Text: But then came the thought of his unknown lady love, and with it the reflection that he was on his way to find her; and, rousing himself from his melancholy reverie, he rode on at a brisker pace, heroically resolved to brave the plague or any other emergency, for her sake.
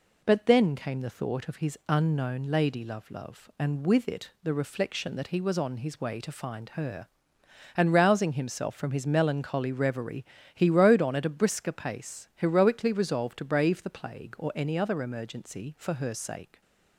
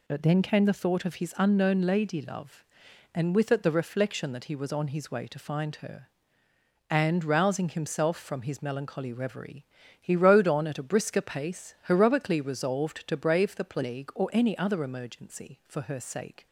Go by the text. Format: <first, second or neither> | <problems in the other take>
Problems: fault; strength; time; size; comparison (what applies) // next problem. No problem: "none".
second | says "love" twice; at 3.1 s